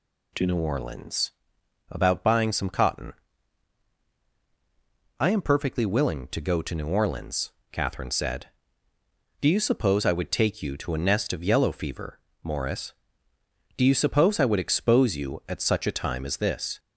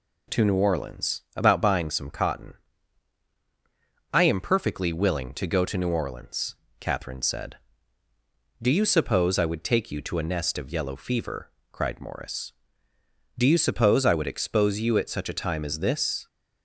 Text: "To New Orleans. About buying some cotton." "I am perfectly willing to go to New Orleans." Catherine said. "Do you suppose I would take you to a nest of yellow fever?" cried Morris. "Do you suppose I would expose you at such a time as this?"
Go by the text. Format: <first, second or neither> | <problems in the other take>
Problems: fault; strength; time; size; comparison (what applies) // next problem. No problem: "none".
second | skips "cried"; at 12.3 s